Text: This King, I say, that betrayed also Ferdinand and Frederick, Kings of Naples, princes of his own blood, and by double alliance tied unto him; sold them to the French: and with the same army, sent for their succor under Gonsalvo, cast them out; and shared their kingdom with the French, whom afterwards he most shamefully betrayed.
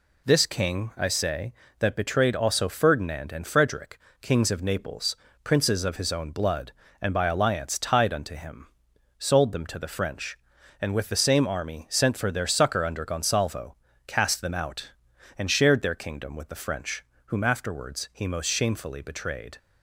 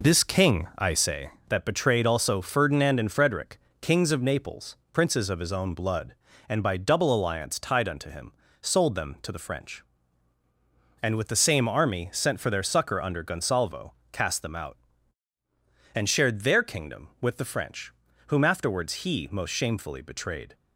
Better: second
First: skips "double"; at 7.2 s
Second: none

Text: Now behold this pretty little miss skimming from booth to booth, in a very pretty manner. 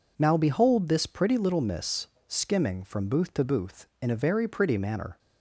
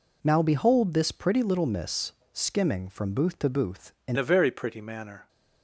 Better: first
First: pauses between "miss" and "skimming"; slight; at 2.0 s; 0.22 s long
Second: pauses between "miss" and "skimming"; slight; at 2.1 s; 0.22 s long // changes voice at "a"; from 4.1 s on; 1.1 s long

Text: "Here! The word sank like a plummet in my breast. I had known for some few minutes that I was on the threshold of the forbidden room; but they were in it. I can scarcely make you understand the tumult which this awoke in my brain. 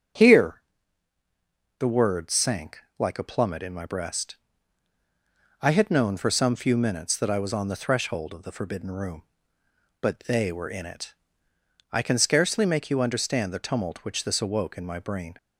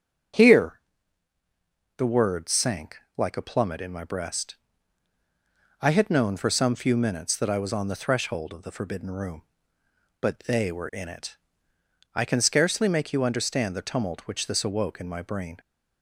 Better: neither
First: starts louder than the rest; strong; until 2.3 s; 7.5 dB // pauses between "sank" and "like"; slight; at 2.8 s; 0.18 s long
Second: starts louder than the rest; strong; until 2.5 s; 7.5 dB // pauses between "sank" and "like"; slight; at 2.9 s; 0.18 s long

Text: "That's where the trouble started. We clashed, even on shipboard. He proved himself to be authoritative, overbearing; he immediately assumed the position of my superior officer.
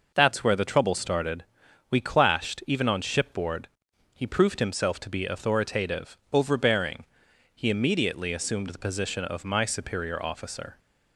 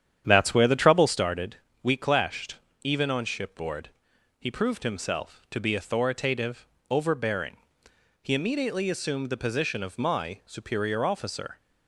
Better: first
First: none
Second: starts louder than the rest; strong; until 1.2 s; 9.5 dB

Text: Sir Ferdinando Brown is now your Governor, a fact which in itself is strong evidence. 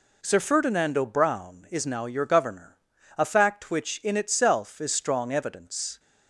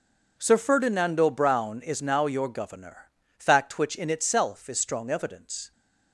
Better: first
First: none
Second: skips "a"; at 3.2 s

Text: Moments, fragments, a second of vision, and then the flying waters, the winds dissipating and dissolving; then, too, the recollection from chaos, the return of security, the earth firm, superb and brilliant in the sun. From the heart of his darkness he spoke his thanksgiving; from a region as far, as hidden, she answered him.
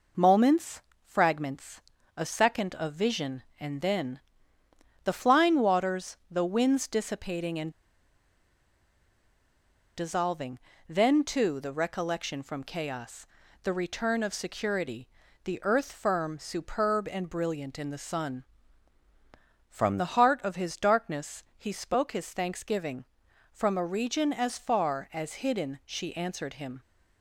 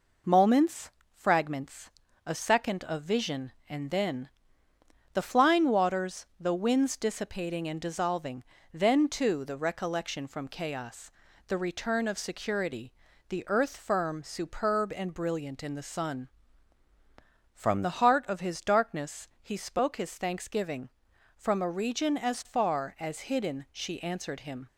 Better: second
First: pauses between "then" and "the"; noticeable; at 4.1 s; 0.84 s long // pauses between "and" and "dissolving"; strong; at 7.6 s; 2.2 s long // pauses between "darkness" and "he"; slight; at 21.4 s; 0.16 s long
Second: pauses between "then" and "the"; noticeable; at 4.2 s; 0.84 s long // pauses between "darkness" and "he"; slight; at 19.2 s; 0.16 s long

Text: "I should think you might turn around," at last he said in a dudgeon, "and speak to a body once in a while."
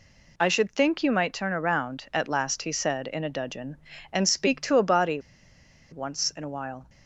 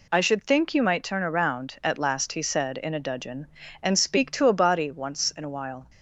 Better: second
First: pauses between "body" and "once"; noticeable; at 5.2 s; 0.69 s long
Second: none

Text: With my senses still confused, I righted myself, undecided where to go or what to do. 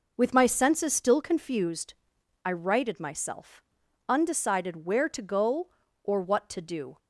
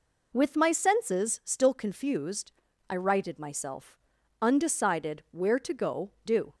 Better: first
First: none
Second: skips "or what to"; at 6.1 s

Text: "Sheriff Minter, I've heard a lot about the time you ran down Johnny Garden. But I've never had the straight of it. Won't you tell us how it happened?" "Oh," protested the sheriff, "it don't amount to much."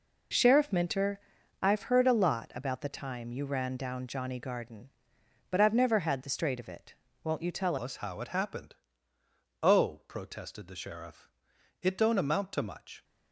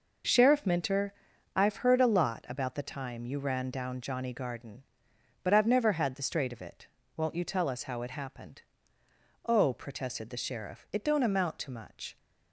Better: second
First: changes voice at "us"; from 7.7 s on; 5.3 s long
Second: none

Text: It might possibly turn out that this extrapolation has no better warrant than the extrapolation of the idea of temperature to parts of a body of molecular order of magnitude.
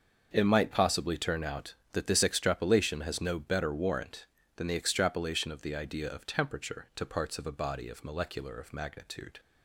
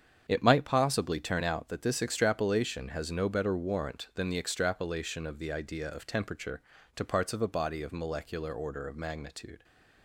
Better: second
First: starts louder than the rest; until 1.3 s; 6.5 dB // skips "order"; at 8.5 s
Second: starts louder than the rest; strong; until 1.2 s; 8 dB

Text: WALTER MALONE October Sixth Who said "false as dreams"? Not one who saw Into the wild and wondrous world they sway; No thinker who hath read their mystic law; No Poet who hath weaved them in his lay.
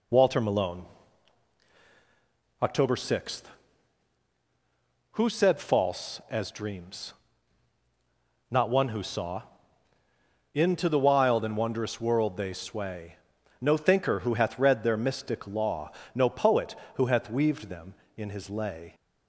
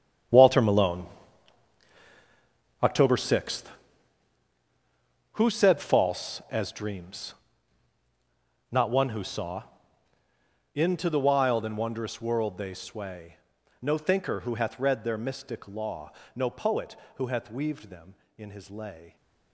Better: first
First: pauses between "MALONE" and "October"; strong; at 0.8 s; 1.7 s long // pauses between "saw" and "Into"; at 9.4 s; 1.1 s long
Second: gets quieter; strong; throughout; 14 dB // pauses between "MALONE" and "October"; strong; at 1.0 s; 1.7 s long // pauses between "saw" and "Into"; at 9.6 s; 1.1 s long

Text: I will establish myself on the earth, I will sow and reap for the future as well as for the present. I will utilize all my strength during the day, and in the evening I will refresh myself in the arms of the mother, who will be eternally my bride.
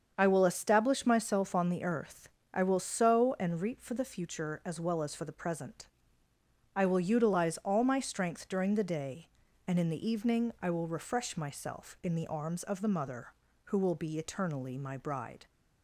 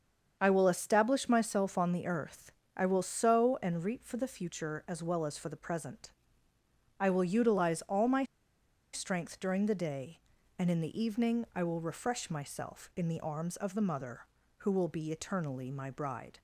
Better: first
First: starts louder than the rest; strong; until 1.1 s; 7 dB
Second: starts louder than the rest; strong; until 1.4 s; 7 dB // pauses between "my" and "strength"; noticeable; at 8.2 s; 0.67 s long

